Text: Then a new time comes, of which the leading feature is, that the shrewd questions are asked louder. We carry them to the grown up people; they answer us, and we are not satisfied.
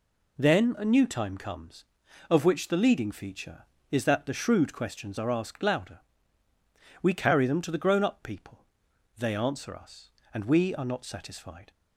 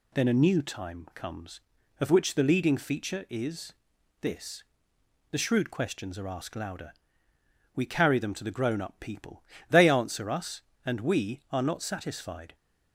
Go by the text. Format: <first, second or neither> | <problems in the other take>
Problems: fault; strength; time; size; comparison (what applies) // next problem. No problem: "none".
first | says "this" for "that"; at 4.2 s